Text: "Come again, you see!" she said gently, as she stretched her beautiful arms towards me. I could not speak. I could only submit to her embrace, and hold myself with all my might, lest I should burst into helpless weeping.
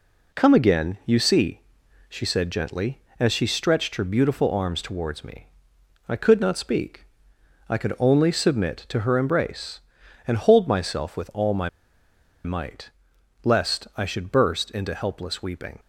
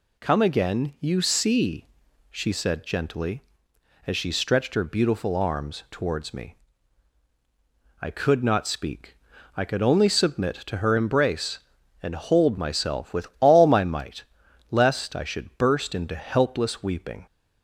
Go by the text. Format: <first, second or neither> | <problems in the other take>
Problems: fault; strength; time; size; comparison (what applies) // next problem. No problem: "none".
second | pauses between "my" and "might"; noticeable; at 11.6 s; 0.76 s long